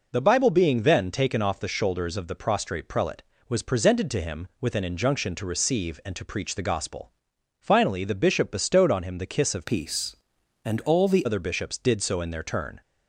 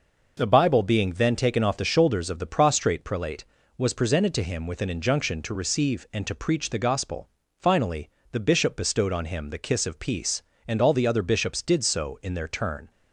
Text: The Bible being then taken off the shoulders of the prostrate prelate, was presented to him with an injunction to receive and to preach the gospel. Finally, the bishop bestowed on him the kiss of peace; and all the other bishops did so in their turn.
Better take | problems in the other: second | changes voice from "peace" to "the"; from 9.6 to 11.2 s; 1.6 s long

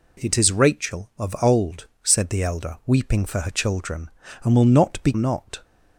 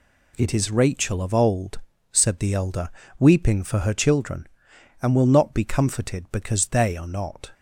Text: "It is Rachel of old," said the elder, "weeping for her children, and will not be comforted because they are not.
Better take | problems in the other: second | skips "comforted because they are"; at 5.1 s

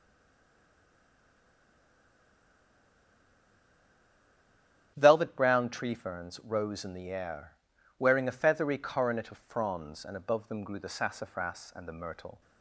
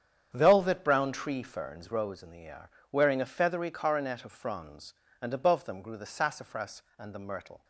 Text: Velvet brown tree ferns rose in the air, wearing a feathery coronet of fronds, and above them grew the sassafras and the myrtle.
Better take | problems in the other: second | stays silent before the first word; strong; until 4.9 s; 4.9 s long // starts louder than the rest; strong; until 5.9 s; 9.5 dB; strong in the second

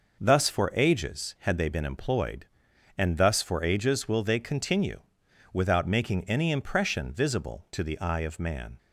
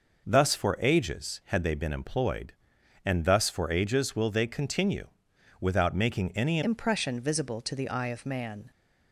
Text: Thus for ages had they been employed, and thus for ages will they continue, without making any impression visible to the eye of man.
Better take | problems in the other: first | changes voice at "impression"; from 6.6 s on; 2.1 s long

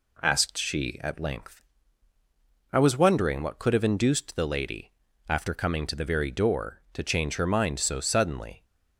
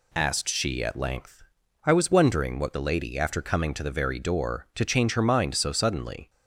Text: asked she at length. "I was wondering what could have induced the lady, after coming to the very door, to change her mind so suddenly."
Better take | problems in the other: first | skips "could have induced"; at 2.7 s

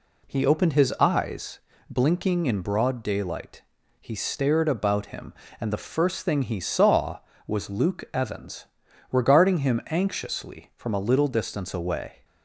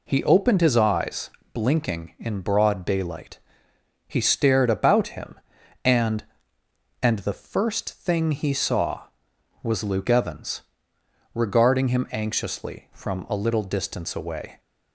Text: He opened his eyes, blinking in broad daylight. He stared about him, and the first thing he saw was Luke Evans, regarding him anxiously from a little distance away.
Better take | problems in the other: first | says "and" twice; at 7.0 s

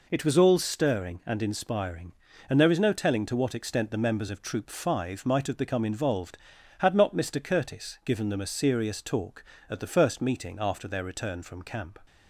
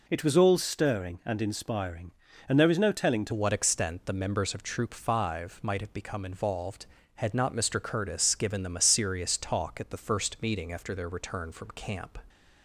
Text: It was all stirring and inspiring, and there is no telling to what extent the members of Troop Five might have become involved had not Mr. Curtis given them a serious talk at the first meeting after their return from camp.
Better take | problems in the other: first | changes voice at "what"; from 3.3 s on; 8.8 s long

